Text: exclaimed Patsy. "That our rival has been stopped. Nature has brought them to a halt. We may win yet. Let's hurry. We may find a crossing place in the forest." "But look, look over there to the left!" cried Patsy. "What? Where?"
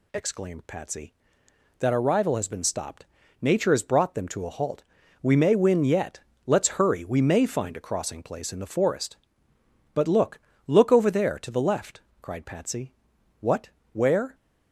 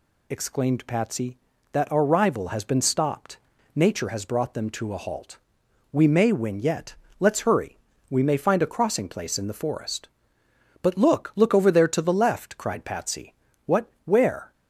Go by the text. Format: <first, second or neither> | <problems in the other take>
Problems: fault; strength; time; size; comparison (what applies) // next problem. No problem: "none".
neither | none